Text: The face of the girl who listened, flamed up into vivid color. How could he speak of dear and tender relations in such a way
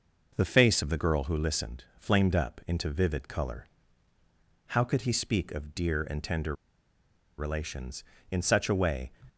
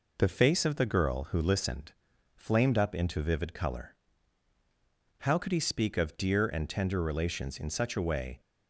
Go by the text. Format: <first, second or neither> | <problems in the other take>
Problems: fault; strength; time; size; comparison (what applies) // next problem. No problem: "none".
second | pauses between "tender" and "relations"; noticeable; at 6.5 s; 0.82 s long